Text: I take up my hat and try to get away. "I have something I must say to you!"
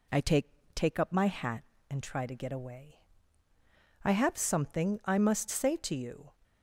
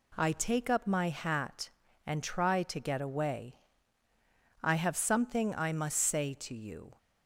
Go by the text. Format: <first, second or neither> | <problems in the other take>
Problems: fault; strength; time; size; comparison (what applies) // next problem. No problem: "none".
second | says "take" twice; at 0.7 s